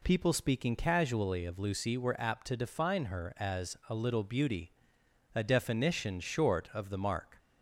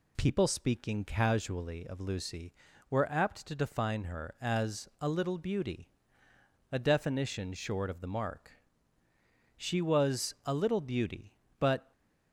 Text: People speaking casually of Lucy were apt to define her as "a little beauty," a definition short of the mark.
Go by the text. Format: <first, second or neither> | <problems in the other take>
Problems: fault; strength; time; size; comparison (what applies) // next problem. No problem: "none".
first | goes on to say "She was a little beauty but"; strong; from 9.5 s on; 2.3 s long